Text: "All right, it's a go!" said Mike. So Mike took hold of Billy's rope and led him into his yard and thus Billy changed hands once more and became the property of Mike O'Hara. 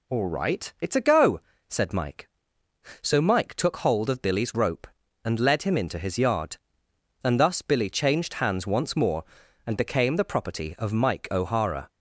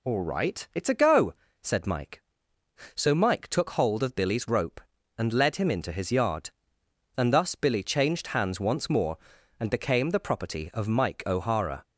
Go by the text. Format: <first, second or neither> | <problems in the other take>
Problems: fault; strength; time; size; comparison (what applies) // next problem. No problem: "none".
neither | none